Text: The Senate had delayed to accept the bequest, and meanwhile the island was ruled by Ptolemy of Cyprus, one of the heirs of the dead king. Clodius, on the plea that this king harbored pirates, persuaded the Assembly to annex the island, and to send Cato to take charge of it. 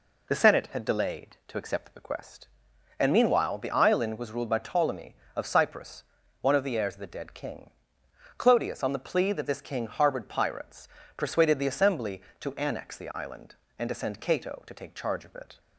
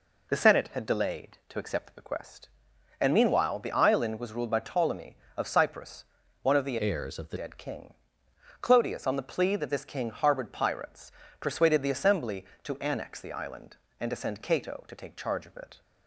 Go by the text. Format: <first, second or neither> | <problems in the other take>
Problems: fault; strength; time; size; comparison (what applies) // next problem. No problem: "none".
first | changes voice from "heirs" to "the"; from 6.8 to 7.3 s; 0.5 s long